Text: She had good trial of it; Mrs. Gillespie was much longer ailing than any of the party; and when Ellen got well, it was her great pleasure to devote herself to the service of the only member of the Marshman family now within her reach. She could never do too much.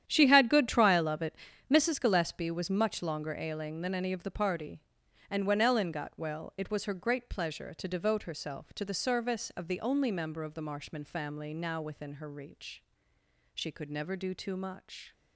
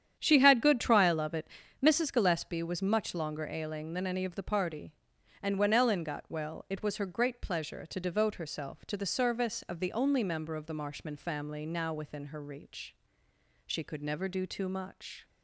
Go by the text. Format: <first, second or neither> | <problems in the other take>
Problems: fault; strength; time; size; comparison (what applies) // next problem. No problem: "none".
second | gets quieter; strong; throughout; 13.5 dB // starts louder than the rest; strong; until 1.0 s; 10 dB; strong in the second